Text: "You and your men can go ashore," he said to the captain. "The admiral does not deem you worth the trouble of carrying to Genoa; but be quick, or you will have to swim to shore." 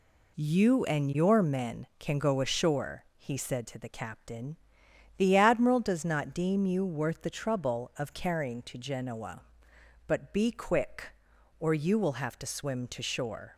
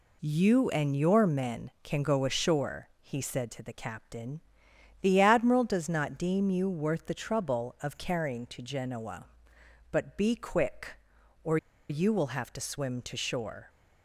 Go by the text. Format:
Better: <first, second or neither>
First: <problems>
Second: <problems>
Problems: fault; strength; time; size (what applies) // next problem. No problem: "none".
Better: first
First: none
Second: pauses between "or" and "you"; slight; at 11.5 s; 0.32 s long